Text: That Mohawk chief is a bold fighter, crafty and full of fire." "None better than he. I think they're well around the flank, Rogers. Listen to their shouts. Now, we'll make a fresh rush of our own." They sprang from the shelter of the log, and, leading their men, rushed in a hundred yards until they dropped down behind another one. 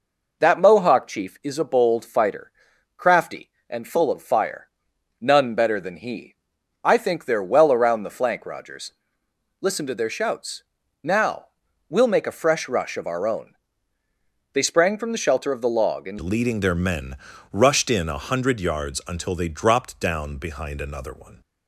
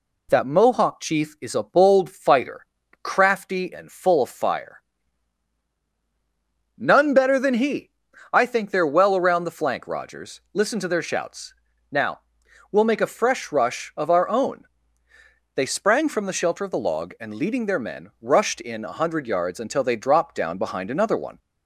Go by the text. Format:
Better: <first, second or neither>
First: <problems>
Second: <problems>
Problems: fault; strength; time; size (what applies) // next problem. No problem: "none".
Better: second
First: changes voice at "leading"; from 16.2 s on; 5.2 s long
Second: none